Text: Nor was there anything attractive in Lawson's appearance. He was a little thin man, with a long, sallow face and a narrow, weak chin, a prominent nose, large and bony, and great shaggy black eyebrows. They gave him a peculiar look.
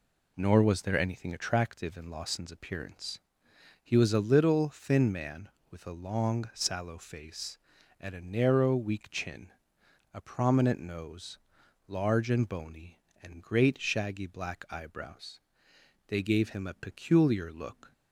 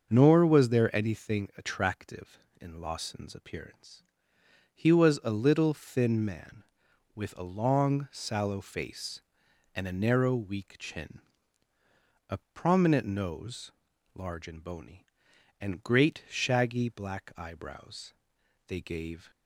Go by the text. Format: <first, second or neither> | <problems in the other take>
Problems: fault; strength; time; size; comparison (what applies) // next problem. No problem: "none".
first | starts louder than the rest; until 1.1 s; 6.5 dB // pauses between "a" and "prominent"; slight; at 12.3 s; 0.16 s long // stops before "him a peculiar look"; at 19.3 s